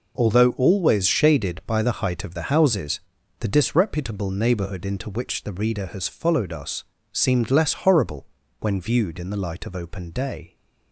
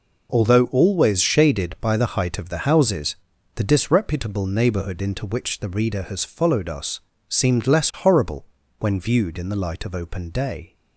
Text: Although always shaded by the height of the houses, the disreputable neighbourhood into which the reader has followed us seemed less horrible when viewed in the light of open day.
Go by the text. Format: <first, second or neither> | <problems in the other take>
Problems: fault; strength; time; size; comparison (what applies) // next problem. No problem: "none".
neither | pauses between "us" and "seemed"; slight; the same in both // pauses between "horrible" and "when"; slight; the same in both